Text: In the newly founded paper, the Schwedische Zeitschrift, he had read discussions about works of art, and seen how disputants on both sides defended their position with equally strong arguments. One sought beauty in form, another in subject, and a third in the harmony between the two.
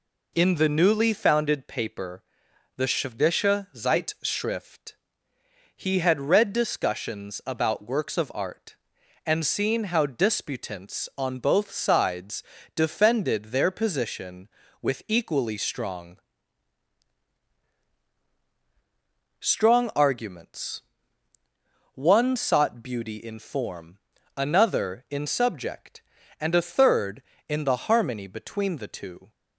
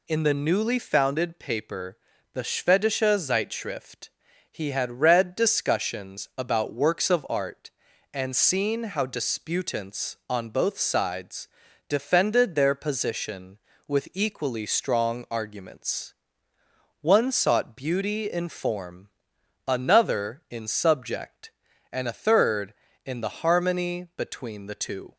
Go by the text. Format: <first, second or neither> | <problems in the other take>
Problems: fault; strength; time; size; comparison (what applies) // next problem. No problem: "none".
second | pauses between "sides" and "defended"; slight; at 12.4 s; 0.32 s long; also in the second // says "strong" twice; at 19.4 s